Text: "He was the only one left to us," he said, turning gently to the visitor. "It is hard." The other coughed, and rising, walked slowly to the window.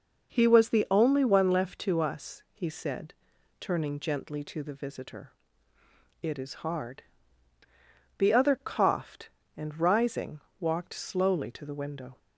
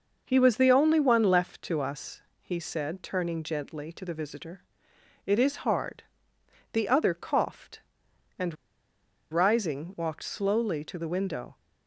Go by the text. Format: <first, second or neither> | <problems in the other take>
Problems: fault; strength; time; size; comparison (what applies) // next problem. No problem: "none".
first | pauses between "and" and "rising"; noticeable; at 8.5 s; 0.76 s long